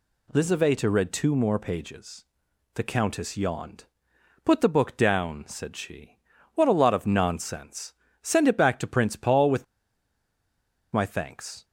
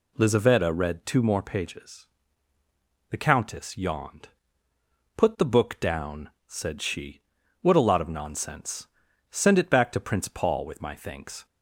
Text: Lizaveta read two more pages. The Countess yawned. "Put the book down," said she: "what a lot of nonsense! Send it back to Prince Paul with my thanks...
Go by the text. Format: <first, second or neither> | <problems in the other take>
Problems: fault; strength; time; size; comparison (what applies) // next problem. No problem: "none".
second | pauses between "with" and "my"; strong; at 9.6 s; 1.2 s long